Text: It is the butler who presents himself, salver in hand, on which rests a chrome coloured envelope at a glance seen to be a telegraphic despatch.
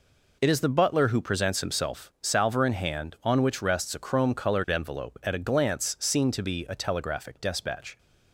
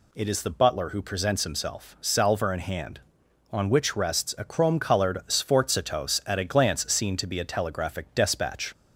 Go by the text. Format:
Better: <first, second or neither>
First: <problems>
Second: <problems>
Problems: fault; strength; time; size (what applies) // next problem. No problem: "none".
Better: first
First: none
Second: says "sforzatos" for "envelope"; at 5.2 s